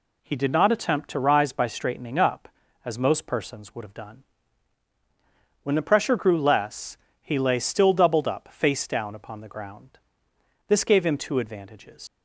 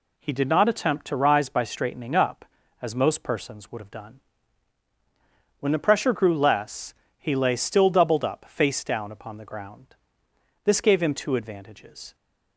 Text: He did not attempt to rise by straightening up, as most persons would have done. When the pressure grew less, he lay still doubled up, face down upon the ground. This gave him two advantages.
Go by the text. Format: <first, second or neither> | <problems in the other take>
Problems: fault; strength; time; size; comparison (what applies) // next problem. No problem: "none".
second | leaves "advantages" unfinished; at 12.0 s; 110 ms